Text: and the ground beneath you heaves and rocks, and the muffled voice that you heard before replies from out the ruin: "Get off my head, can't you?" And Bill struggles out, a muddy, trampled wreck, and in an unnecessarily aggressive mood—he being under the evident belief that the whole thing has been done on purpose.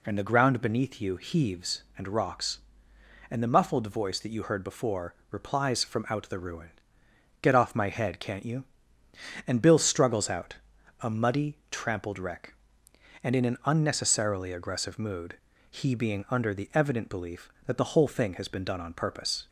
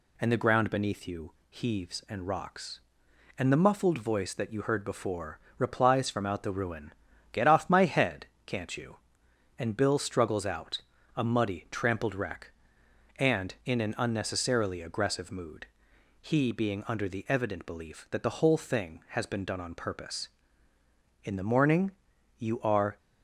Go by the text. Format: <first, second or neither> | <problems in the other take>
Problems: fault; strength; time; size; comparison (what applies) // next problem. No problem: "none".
first | pauses between "you" and "heaves"; slight; at 1.3 s; 0.16 s long // pauses between "before" and "replies"; slight; at 5.3 s; 0.20 s long; slight in the first // goes on to say "In the morning you are"; strong; from 21.2 s on; 1.7 s long